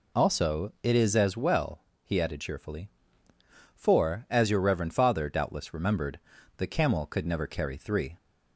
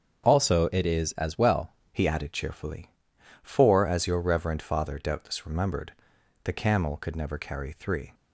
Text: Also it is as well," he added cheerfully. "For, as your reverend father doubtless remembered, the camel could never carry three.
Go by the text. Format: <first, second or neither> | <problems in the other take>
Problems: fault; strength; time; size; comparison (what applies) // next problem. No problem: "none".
first | starts louder than the rest; strong; until 1.2 s; 7.5 dB // changes voice at "he"; from 1.9 s on; 6.2 s long